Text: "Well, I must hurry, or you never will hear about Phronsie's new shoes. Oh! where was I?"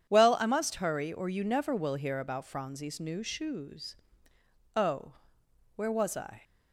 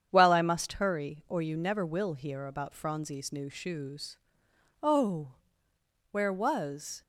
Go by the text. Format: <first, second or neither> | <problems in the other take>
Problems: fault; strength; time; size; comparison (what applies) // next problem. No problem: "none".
first | starts louder than the rest; strong; until 1.1 s; 8 dB // stops before "I"; at 7.0 s